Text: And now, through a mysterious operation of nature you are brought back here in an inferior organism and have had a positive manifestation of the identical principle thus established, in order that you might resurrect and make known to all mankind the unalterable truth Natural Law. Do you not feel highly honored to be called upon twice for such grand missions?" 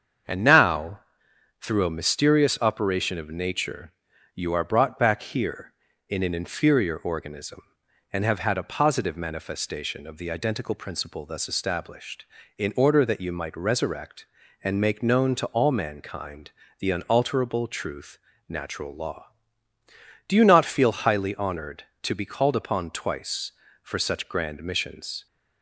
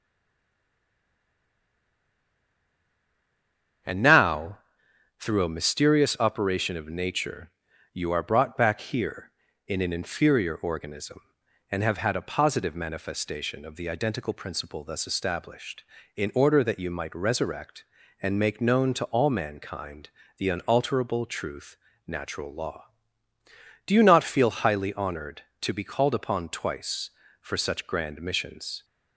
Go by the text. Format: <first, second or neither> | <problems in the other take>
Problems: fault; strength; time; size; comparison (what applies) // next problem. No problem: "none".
first | stays silent before the first word; strong; until 3.8 s; 3.8 s long // starts louder than the rest; strong; until 5.4 s; 7.5 dB; strong in the first // pauses between "nature" and "you"; at 7.5 s; 0.44 s long; also in the first // pauses between "mankind" and "the"; slight; at 20.0 s; 0.30 s long; slight in the first // pauses between "truth" and "Natural"; slight; at 21.7 s; 0.30 s long; slight in the first